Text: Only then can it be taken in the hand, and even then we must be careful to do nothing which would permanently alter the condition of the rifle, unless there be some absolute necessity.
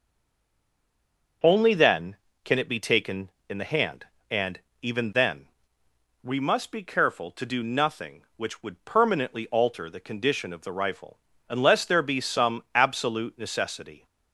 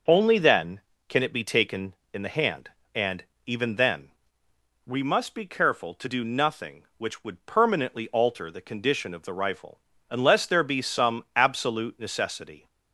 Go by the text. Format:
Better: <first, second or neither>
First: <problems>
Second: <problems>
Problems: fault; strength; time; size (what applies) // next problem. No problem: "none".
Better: second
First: stays silent before the first word; noticeable; until 1.4 s; 1.4 s long // pauses between "and" and "even"; slight; at 4.6 s; 0.20 s long // pauses between "then" and "we"; noticeable; at 5.4 s; 0.78 s long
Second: pauses between "and" and "even"; slight; at 3.2 s; 0.20 s long // pauses between "then" and "we"; noticeable; at 4.0 s; 0.78 s long